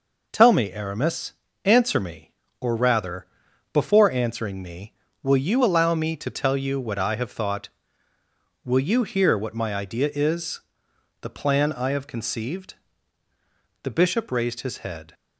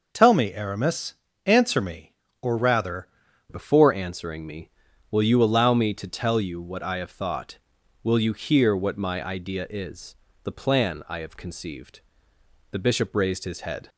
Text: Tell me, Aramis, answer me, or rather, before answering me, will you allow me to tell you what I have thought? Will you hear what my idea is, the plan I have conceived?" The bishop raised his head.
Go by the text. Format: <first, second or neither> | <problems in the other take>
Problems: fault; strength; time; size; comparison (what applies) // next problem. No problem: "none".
first | changes voice at "before"; from 3.4 s on; 10.4 s long